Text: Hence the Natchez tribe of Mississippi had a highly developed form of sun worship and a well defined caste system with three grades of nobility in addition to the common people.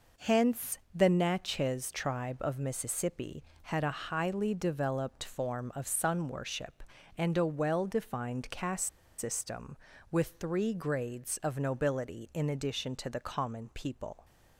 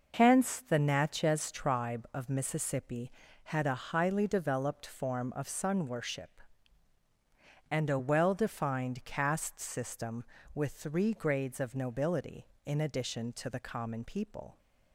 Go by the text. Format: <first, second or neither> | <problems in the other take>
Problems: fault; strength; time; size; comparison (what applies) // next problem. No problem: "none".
second | pauses between "Hence" and "the"; slight; at 0.7 s; 0.16 s long // pauses between "caste" and "system"; slight; at 8.8 s; 0.30 s long